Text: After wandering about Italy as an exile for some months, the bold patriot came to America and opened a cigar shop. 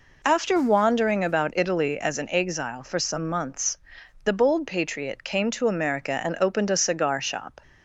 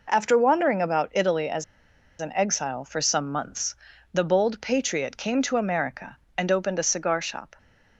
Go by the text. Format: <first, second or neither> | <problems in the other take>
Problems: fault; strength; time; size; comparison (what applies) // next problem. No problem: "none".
first | pauses between "as" and "an"; noticeable; at 1.6 s; 0.57 s long